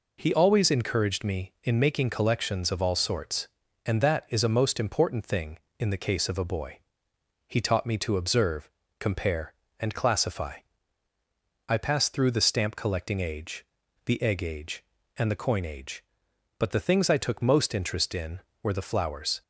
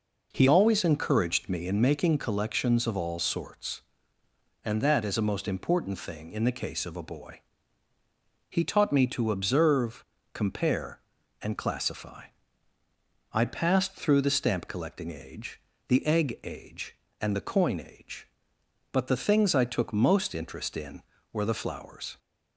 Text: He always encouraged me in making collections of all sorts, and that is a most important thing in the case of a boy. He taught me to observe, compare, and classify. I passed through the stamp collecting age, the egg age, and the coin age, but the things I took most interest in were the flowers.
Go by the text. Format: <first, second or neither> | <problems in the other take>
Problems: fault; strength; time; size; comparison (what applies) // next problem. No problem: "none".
first | changes voice at "always"; from 0.4 s on; 21.7 s long